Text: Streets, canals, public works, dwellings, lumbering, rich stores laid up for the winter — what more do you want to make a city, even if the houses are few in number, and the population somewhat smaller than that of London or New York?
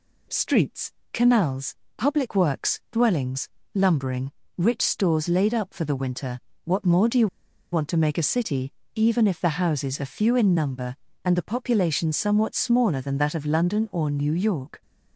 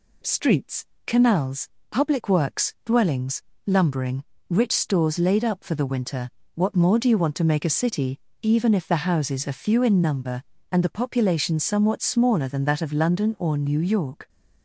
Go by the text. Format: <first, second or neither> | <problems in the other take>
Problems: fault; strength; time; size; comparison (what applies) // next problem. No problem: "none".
second | pauses between "you" and "want"; noticeable; at 7.2 s; 0.46 s long